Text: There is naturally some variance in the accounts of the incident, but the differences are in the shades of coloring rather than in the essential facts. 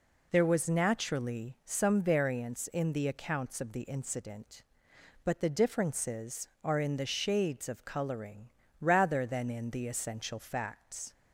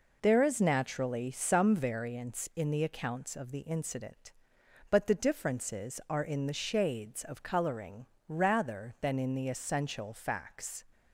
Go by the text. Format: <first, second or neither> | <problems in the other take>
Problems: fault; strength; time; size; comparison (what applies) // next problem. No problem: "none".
second | says "was" for "is"; at 0.4 s // pauses between "coloring" and "rather"; slight; at 8.4 s; 0.30 s long; slight in the second